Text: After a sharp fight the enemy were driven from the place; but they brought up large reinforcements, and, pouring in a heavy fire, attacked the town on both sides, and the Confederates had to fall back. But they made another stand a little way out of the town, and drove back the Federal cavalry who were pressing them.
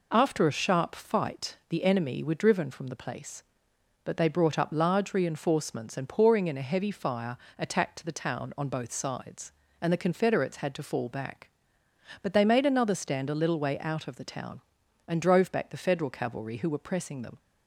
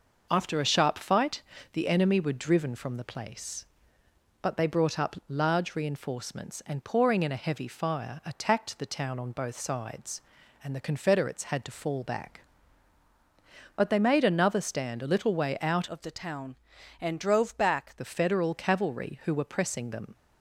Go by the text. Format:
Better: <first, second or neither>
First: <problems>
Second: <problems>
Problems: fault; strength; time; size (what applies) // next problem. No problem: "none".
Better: first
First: none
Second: pauses between "fight" and "the"; slight; at 1.4 s; 0.32 s long // changes voice from "of" to "back"; from 15.8 to 17.9 s; 2.1 s long